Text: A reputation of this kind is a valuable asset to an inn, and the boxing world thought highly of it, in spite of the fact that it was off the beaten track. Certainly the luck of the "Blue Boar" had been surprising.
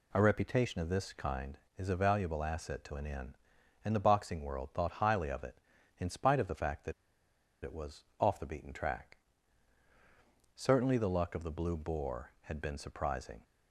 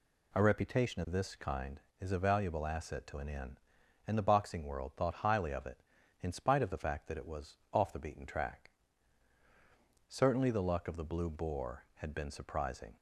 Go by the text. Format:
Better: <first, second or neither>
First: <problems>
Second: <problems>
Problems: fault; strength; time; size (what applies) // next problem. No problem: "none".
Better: second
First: pauses between "that" and "it"; noticeable; at 6.9 s; 0.70 s long // pauses between "was" and "off"; slight; at 8.0 s; 0.16 s long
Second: pauses between "was" and "off"; slight; at 7.5 s; 0.16 s long